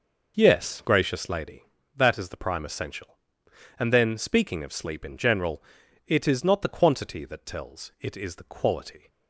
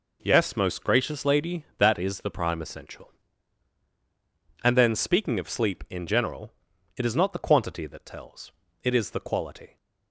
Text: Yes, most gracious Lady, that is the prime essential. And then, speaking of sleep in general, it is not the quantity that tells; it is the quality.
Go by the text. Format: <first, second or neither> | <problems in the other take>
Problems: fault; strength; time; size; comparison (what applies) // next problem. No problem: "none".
second | skips "most"; at 0.8 s